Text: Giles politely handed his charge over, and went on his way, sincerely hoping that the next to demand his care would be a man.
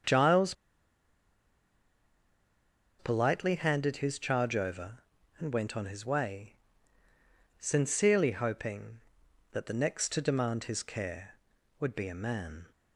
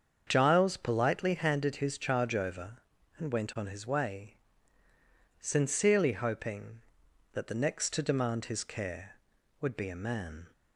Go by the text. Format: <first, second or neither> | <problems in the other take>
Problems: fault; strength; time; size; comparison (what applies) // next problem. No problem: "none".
second | starts louder than the rest; strong; until 3.5 s; 7 dB; strong in the second // pauses between "Giles" and "politely"; strong; at 0.5 s; 2.4 s long